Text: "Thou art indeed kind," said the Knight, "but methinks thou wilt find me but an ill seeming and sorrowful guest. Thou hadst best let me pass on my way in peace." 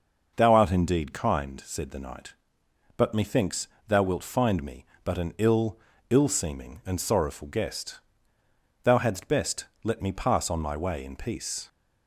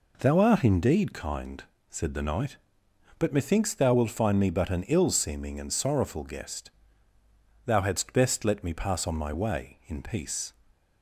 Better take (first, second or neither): second